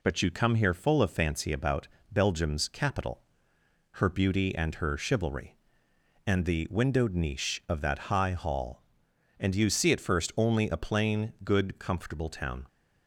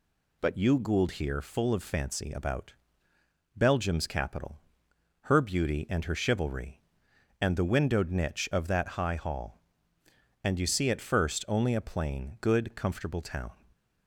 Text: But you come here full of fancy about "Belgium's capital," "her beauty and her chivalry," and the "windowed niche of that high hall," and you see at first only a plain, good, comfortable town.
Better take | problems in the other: first | says "gould" for "come"; at 0.7 s // pauses between "about" and "Belgium's"; noticeable; at 2.7 s; 0.84 s long; slight in the first

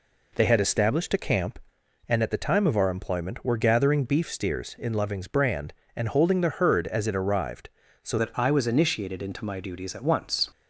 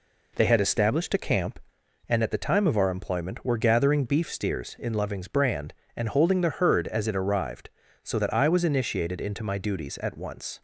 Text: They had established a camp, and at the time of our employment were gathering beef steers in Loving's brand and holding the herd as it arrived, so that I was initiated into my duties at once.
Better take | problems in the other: second | changes voice at "that"; from 8.1 s on; 2.4 s long

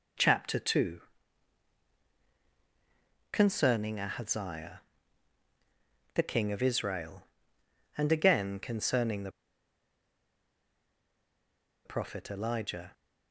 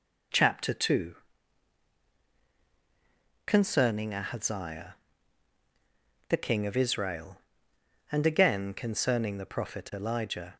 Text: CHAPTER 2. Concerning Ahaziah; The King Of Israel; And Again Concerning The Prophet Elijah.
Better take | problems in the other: second | pauses between "The" and "Prophet"; strong; at 9.2 s; 2.5 s long

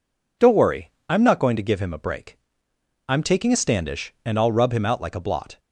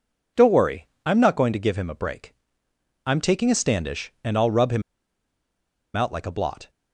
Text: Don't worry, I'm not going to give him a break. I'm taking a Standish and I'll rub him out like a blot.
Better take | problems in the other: first | pauses between "him" and "out"; at 4.8 s; 1.1 s long

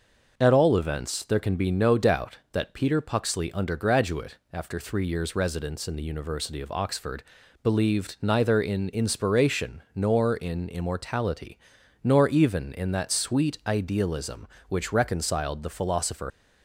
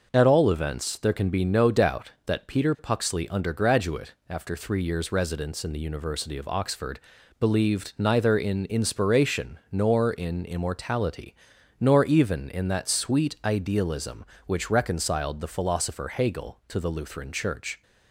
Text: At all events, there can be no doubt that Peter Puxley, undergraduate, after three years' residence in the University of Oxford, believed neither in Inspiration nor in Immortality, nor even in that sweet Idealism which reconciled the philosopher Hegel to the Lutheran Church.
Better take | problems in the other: second | starts louder than the rest; noticeable; until 1.3 s; 6 dB // stops before "Hegel to the Lutheran Church"; at 16.3 s

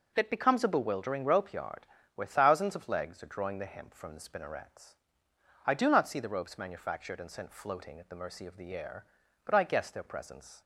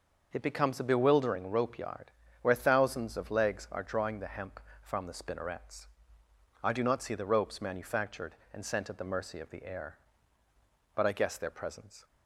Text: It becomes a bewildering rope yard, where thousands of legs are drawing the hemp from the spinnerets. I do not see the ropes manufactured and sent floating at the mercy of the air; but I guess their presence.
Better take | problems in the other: first | starts louder than the rest; noticeable; until 1.3 s; 6 dB; noticeable in the first // skips "floating"; at 8.8 s

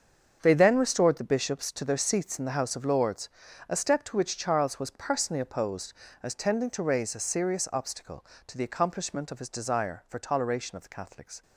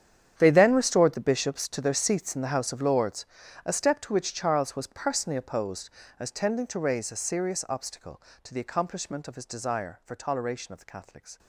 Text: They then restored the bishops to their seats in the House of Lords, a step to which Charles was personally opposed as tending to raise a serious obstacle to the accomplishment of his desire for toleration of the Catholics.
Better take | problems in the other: first | gets quieter; strong; throughout; 17 dB // starts louder than the rest; strong; until 1.3 s; 9 dB; also in the first

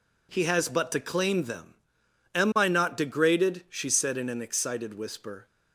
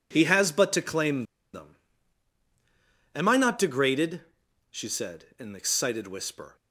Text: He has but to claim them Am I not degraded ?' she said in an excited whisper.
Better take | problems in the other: first | pauses between "claim" and "them"; slight; at 1.2 s; 0.30 s long // pauses between "them" and "Am"; strong; at 1.7 s; 1.3 s long; noticeable in the first

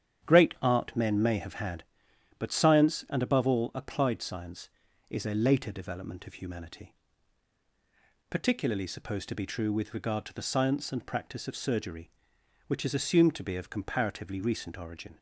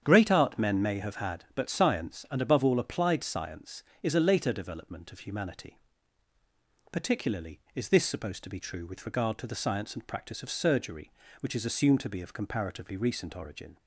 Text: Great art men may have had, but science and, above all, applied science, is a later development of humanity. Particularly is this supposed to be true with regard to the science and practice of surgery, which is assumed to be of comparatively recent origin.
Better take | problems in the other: second | starts louder than the rest; strong; until 1.3 s; 9 dB; strong in the second // skips "is this"; at 8.8 s

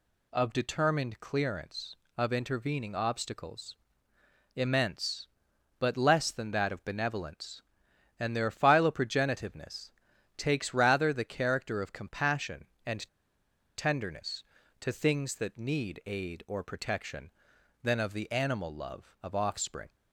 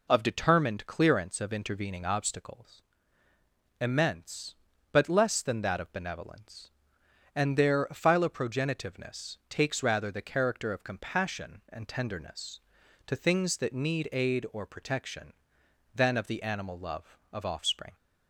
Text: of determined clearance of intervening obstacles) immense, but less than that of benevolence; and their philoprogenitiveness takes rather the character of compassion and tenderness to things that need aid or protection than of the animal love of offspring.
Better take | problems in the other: second | pauses between "philoprogenitiveness" and "takes"; at 9.9 s; 0.44 s long // pauses between "and" and "tenderness"; noticeable; at 13.0 s; 0.68 s long

